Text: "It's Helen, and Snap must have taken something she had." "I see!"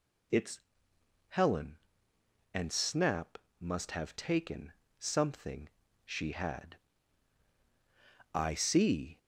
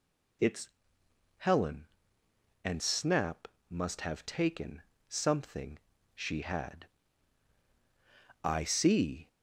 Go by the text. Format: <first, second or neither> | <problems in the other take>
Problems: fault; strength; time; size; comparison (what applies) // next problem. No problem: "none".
neither | pauses between "It's" and "Helen"; noticeable; the same in both // pauses between "Snap" and "must"; slight; the same in both // pauses between "taken" and "something"; slight; the same in both // pauses between "something" and "she"; slight; the same in both